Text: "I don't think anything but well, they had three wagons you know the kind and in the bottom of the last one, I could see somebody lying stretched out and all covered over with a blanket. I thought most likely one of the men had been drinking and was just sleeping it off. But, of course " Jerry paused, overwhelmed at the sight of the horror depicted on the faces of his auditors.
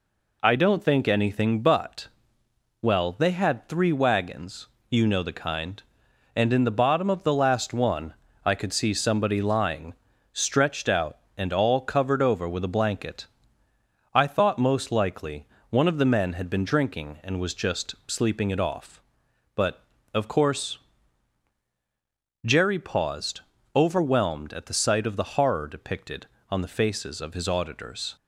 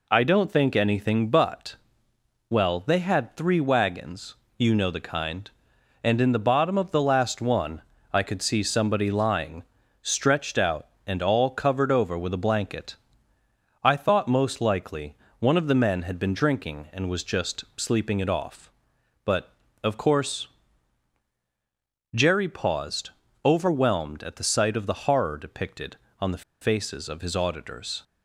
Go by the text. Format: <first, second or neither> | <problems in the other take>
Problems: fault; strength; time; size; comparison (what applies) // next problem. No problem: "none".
first | pauses between "but" and "well"; noticeable; at 1.7 s; 0.72 s long; noticeable in the first // pauses between "wagons" and "you"; slight; at 4.3 s; 0.20 s long; slight in the first // pauses between "lying" and "stretched"; at 9.6 s; 0.40 s long; also in the first // pauses between "likely" and "one"; slight; at 15.1 s; 0.24 s long; slight in the first // pauses between "the" and "faces"; slight; at 26.4 s; 0.19 s long